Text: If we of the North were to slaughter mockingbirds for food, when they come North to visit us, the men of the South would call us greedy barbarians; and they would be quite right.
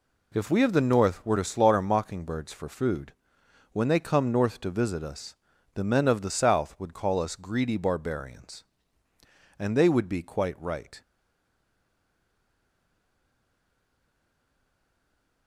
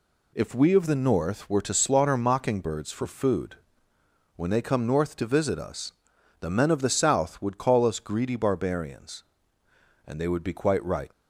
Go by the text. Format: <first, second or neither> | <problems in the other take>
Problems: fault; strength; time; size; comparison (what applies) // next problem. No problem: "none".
second | stays silent after the last word; strong; from 11.0 s on; 4.4 s long